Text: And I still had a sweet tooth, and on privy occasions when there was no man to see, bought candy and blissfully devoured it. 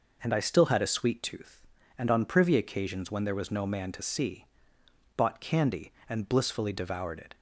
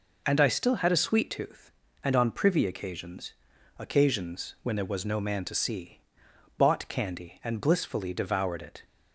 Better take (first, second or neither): first